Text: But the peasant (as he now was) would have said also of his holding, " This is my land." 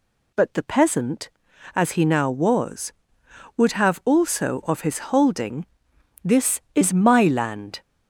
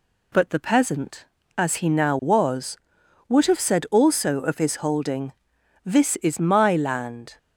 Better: second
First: skips "said"; at 4.0 s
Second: none

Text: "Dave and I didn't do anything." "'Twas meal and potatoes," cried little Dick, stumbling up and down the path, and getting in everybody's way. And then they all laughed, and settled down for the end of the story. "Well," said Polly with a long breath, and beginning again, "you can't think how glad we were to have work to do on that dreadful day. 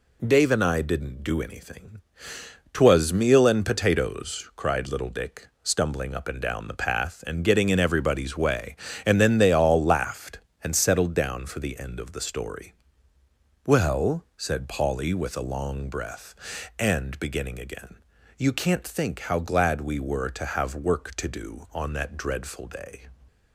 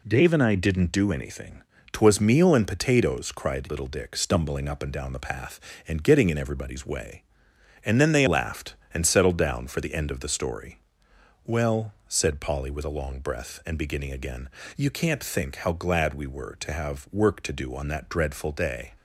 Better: first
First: none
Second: skips "all"; at 8.2 s

